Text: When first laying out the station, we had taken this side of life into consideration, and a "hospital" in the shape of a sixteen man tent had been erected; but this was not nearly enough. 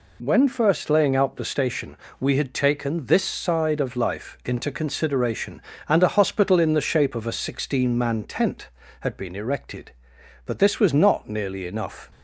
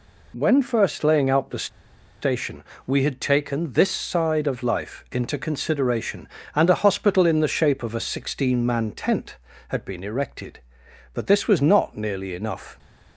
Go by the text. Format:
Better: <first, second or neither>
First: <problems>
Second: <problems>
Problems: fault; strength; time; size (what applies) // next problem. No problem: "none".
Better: first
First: none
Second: pauses between "the" and "station"; noticeable; at 1.6 s; 0.54 s long